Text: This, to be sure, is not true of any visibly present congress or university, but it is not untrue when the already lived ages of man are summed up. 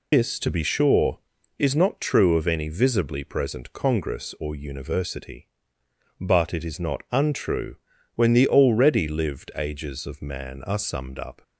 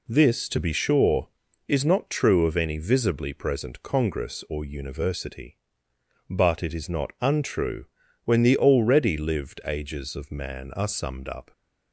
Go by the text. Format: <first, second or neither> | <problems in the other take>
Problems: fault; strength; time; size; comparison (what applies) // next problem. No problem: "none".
second | loses the start of "This"; at 0.1 s; 140 ms // pauses between "untrue" and "when"; at 7.7 s; 0.40 s long; also in the second